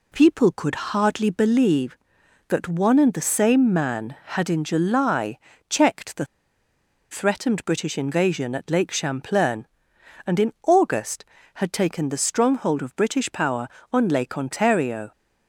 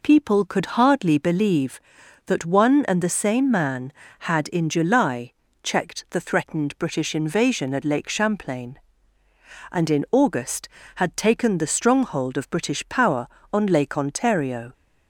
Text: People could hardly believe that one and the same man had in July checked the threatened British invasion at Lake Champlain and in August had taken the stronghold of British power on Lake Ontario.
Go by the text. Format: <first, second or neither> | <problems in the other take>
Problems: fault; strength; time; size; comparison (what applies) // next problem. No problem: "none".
second | pauses between "July" and "checked"; slight; at 5.3 s; 0.32 s long; slight in the second // pauses between "the" and "threatened"; noticeable; at 6.2 s; 0.86 s long